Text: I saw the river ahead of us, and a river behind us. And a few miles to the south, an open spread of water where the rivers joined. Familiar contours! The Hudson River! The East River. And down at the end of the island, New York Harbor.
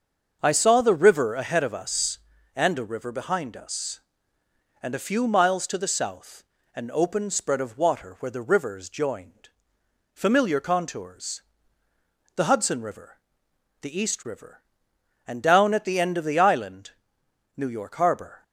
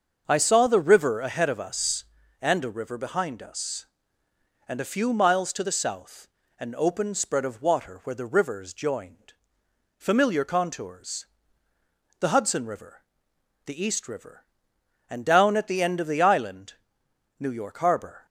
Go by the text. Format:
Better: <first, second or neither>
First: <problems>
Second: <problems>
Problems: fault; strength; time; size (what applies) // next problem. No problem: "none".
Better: neither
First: starts louder than the rest; until 1.4 s; 6.5 dB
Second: starts louder than the rest; until 1.2 s; 6.5 dB